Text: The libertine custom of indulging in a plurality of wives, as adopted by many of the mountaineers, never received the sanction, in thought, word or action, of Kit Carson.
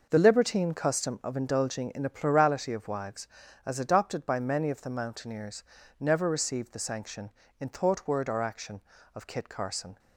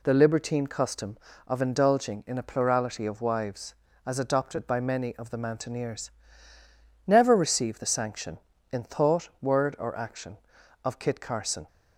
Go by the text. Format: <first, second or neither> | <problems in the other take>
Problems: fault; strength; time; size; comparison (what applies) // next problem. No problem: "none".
neither | none